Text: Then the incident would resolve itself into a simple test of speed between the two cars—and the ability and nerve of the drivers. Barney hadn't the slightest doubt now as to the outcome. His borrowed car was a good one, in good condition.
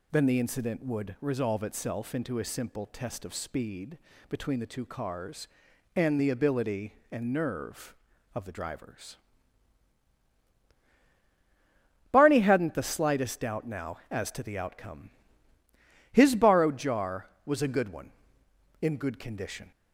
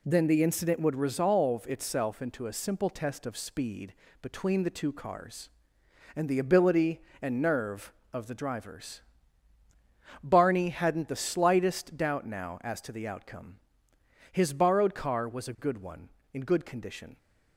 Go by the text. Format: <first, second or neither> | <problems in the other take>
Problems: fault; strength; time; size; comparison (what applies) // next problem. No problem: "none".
second | pauses between "speed" and "between"; slight; at 3.9 s; 0.32 s long; slight in the second // says "jar" for "car"; at 16.7 s